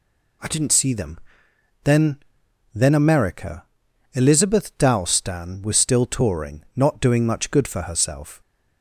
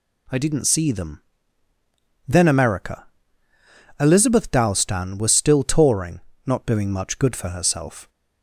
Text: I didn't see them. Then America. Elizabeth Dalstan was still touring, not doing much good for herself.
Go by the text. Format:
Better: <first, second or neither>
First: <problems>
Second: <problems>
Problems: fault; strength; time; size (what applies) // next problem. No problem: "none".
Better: second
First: says "Then" twice; at 2.7 s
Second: none